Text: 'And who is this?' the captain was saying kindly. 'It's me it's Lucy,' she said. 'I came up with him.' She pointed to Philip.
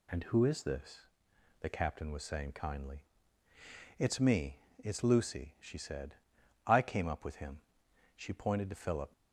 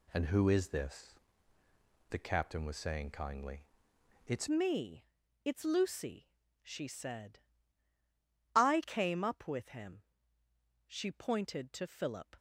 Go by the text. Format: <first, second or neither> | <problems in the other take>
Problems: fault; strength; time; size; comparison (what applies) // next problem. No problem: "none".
first | changes voice at "me"; from 4.5 s on; 7.8 s long // pauses between "me" and "it's"; at 5.0 s; 0.38 s long; slight in the first